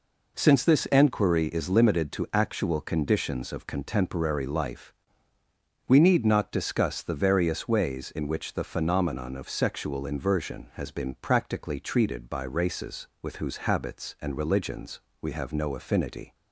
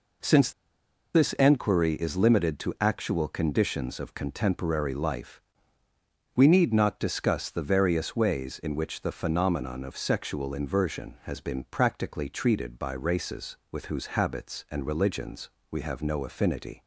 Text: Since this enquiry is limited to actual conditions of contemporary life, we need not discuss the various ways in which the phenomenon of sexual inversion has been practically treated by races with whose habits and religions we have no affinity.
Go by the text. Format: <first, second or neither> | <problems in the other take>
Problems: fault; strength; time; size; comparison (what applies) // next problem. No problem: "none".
first | pauses between "Since" and "this"; noticeable; at 0.5 s; 0.63 s long // pauses between "religions" and "we"; slight; at 15.4 s; 0.20 s long; slight in the first